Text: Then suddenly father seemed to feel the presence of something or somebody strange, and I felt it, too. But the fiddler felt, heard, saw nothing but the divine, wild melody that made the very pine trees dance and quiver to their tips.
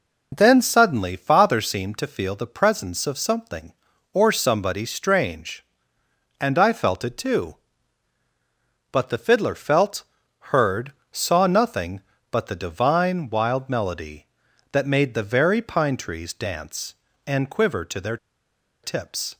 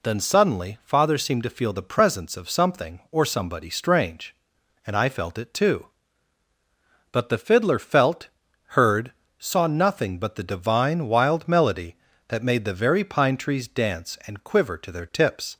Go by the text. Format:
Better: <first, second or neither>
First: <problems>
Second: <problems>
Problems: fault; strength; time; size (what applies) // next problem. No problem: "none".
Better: second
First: pauses between "their" and "tips"; noticeable; at 18.1 s; 0.66 s long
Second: none